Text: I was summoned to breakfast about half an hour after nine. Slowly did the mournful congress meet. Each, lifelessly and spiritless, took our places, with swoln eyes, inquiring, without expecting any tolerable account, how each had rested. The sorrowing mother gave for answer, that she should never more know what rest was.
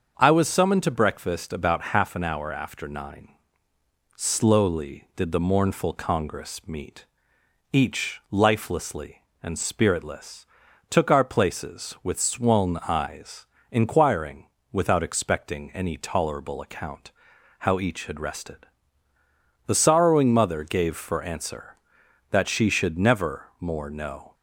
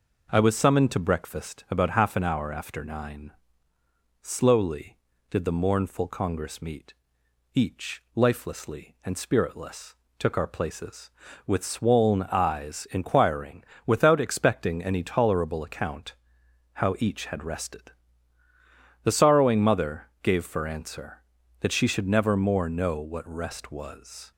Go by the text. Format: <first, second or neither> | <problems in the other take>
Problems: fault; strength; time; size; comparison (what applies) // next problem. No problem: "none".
second | starts louder than the rest; until 1.1 s; 6.5 dB // stops before "what rest was"; at 24.3 s